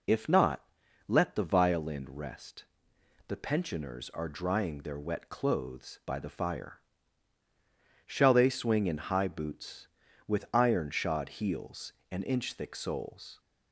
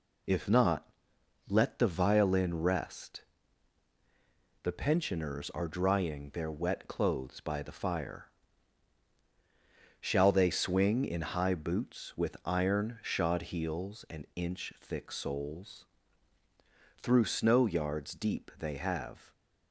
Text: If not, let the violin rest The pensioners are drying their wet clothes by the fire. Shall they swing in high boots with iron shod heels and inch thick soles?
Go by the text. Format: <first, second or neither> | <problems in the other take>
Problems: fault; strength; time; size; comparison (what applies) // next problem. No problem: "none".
first | pauses between "rest" and "The"; strong; at 3.2 s; 1.3 s long; noticeable in the first // goes on to say "Through snow yards deep they have"; strong; from 16.9 s on; 2.3 s long